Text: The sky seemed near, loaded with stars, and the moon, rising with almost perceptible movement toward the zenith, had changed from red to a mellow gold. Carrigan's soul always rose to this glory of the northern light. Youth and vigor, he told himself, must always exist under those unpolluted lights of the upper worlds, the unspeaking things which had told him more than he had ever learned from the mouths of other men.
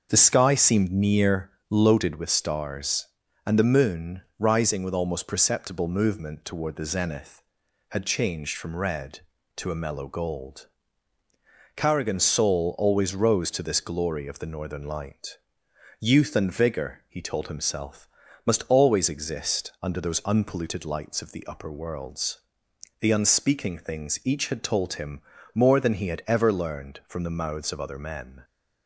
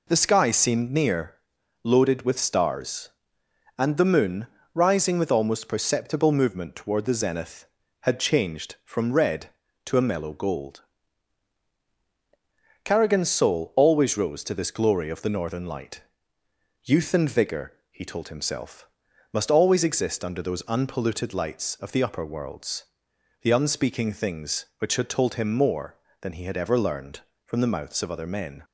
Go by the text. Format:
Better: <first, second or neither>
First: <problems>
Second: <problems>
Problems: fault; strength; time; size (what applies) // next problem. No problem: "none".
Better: second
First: starts louder than the rest; until 1.1 s; 6.5 dB // says "each" for "which"; at 24.2 s // pauses between "him" and "more"; slight; at 25.1 s; 0.34 s long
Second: none